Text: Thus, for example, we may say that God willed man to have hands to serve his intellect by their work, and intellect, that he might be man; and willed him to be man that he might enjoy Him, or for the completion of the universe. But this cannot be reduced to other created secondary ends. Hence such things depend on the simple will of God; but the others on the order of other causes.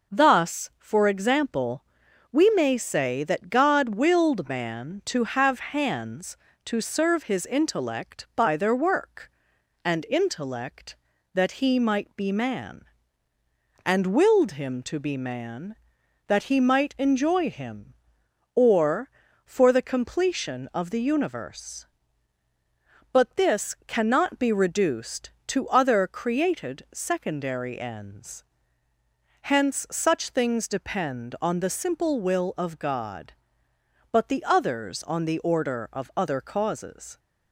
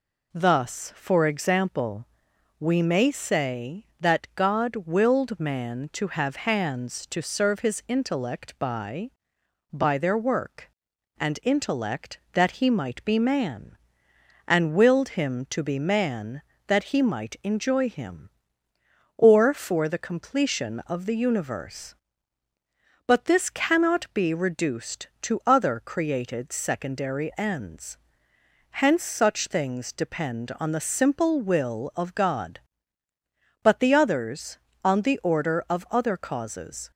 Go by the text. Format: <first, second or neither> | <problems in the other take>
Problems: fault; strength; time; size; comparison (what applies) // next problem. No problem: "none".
first | says "by" twice; at 9.7 s